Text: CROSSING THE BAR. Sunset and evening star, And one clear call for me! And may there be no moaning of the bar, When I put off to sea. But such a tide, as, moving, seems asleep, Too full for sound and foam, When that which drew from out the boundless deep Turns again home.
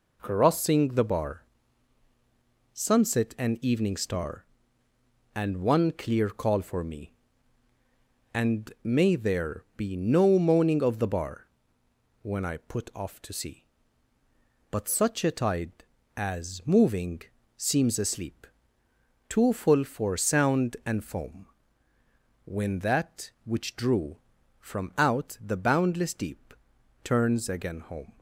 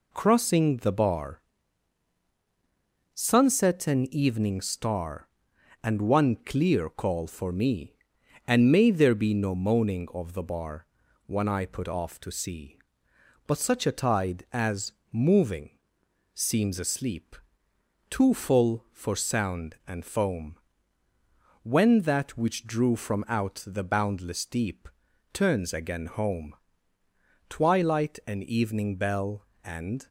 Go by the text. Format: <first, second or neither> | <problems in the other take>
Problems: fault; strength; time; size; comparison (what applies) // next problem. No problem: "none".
first | pauses between "deep" and "Turns"; at 24.8 s; 0.44 s long; noticeable in the first // goes on to say "Twilight and evening bell And"; strong; from 27.4 s on; 2.6 s long